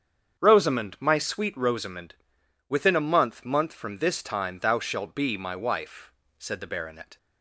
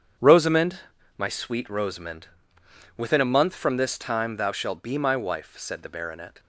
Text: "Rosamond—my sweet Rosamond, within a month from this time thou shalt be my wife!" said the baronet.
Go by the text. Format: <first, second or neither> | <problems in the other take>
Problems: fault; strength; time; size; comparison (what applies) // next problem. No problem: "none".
second | starts louder than the rest; strong; until 1.4 s; 7.5 dB; strong in the second // says "month" twice; at 3.4 s